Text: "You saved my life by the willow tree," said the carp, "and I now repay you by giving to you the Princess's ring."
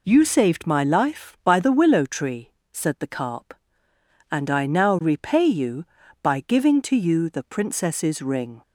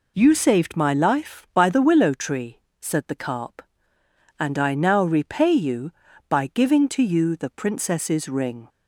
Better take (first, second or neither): neither